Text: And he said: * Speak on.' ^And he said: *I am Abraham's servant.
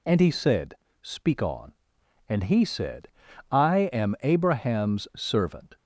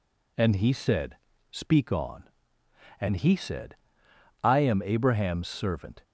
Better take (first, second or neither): neither